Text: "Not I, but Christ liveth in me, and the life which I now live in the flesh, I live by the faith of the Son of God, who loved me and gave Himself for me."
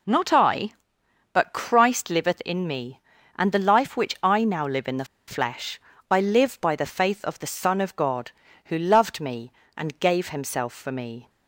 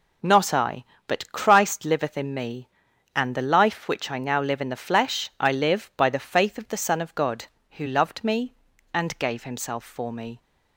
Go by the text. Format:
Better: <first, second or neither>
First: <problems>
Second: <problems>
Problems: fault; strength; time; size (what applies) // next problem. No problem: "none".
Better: second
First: pauses between "the" and "flesh"; slight; at 5.0 s; 0.23 s long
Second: none